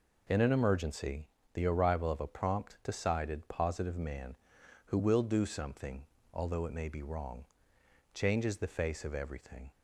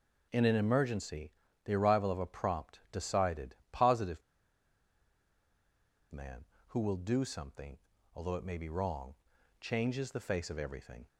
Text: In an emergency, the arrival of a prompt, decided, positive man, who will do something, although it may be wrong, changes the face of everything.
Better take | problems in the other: first | pauses between "positive" and "man"; strong; at 4.2 s; 1.9 s long

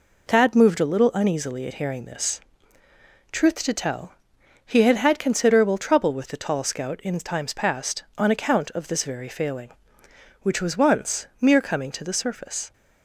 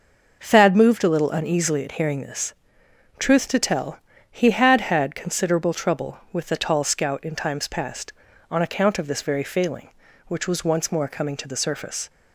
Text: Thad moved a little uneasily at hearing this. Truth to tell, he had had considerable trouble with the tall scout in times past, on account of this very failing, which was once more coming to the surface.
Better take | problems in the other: second | says "mere" for "more"; at 11.4 s

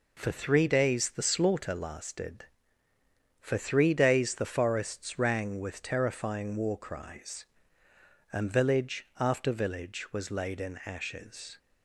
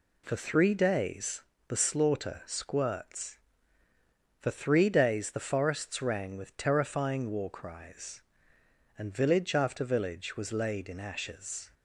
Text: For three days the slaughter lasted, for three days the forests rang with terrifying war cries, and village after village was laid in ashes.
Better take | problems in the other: first | pauses between "days" and "the"; slight; at 1.4 s; 0.26 s long // says "squirts" for "lasted"; at 2.4 s

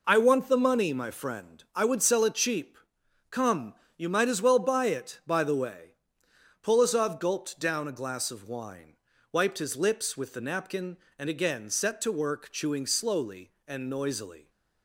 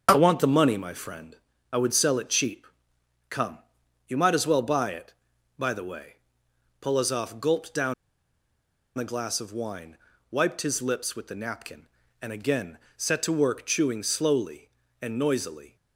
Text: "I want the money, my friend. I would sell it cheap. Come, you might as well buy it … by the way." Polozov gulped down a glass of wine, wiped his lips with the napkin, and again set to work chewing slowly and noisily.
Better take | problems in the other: first | starts louder than the rest; until 1.1 s; 7 dB // pauses between "down" and "a"; at 7.9 s; 1.0 s long // pauses between "again" and "set"; slight; at 12.7 s; 0.18 s long

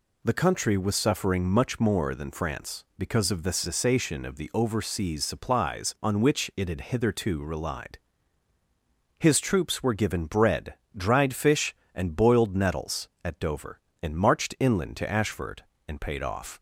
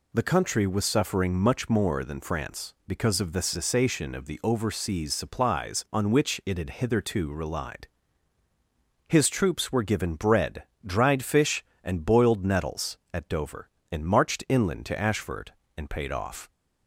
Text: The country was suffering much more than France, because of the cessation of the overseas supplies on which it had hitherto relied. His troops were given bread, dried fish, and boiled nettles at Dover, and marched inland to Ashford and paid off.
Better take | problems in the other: neither | none

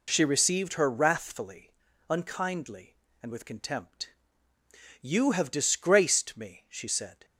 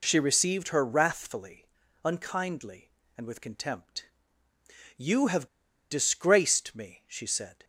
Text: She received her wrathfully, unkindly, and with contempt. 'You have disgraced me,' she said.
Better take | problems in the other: first | pauses between "have" and "disgraced"; at 5.4 s; 0.45 s long

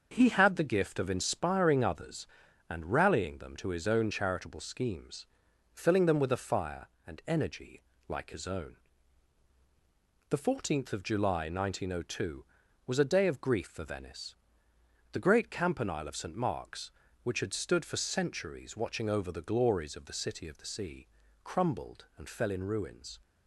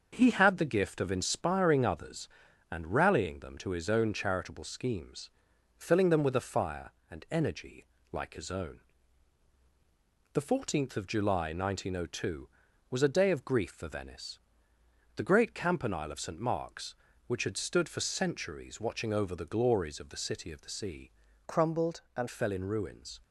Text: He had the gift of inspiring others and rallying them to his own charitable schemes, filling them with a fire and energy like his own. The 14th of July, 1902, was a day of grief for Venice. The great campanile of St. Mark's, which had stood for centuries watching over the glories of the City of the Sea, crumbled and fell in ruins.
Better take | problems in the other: first | starts louder than the rest; until 1.1 s; 6.5 dB; also in the first // pauses between "energy" and "like"; slight; at 7.8 s; 0.24 s long; slight in the first // changes voice from "crumbled" to "and"; from 21.4 to 22.2 s; 0.8 s long

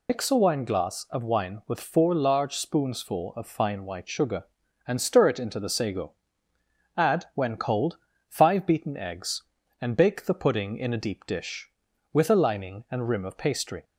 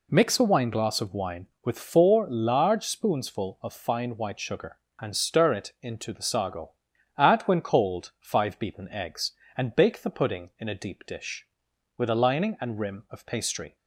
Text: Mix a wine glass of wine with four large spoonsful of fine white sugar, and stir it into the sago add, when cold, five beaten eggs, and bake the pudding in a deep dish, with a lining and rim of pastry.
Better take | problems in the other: second | loses the start of "Mix"; at 0.0 s; 120 ms // pauses between "sago" and "add"; noticeable; at 6.1 s; 0.86 s long; also in the second

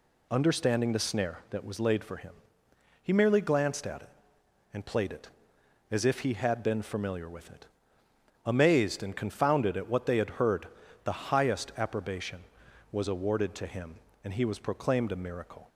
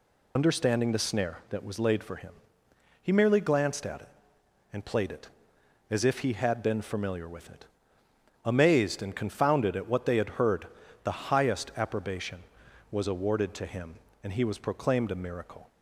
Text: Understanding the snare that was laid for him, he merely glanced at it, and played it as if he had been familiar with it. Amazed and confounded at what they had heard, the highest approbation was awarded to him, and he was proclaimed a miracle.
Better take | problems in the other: first | loses the start of "Understanding"; at 0.3 s; 55 ms

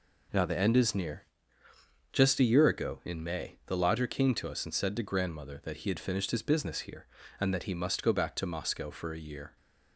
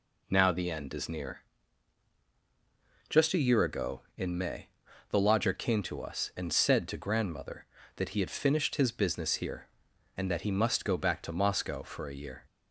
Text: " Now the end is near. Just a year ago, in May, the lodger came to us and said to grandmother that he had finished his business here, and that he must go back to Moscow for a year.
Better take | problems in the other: neither | none

